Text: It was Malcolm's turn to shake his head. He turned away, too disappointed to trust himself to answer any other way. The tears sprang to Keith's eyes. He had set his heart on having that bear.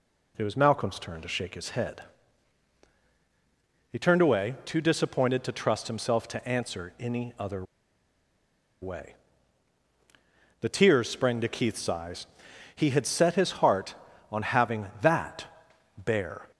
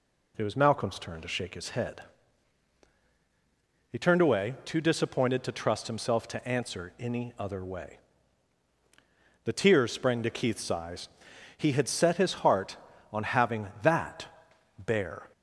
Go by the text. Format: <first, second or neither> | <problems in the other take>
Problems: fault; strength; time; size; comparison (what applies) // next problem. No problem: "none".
second | pauses between "other" and "way"; at 7.6 s; 1.1 s long // pauses between "that" and "bear"; noticeable; at 15.4 s; 0.52 s long; noticeable in the second